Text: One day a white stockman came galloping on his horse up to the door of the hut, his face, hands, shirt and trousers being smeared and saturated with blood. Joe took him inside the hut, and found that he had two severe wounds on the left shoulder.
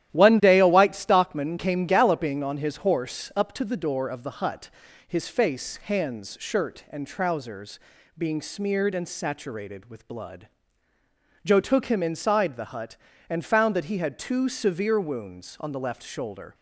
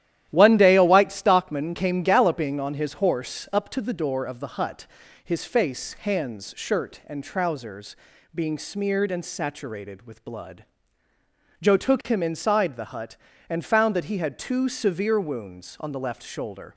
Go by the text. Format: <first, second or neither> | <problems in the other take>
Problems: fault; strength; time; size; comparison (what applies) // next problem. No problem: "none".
neither | starts louder than the rest; strong; the same in both // pauses between "trousers" and "being"; the same in both